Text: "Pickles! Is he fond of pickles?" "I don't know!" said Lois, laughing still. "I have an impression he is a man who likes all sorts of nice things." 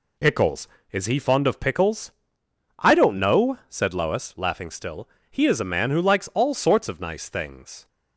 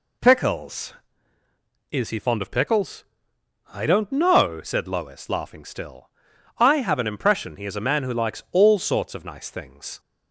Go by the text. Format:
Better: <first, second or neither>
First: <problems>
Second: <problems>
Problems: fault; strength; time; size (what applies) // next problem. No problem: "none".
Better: second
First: skips "I have an impression"; at 5.1 s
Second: none